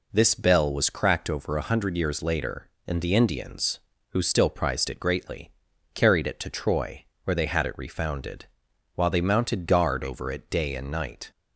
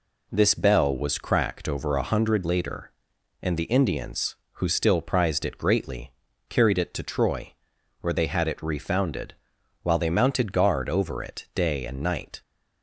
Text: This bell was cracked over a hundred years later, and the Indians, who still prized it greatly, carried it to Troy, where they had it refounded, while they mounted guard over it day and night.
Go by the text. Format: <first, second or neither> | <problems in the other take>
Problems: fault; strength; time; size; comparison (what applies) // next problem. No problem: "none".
first | skips "years"; at 2.4 s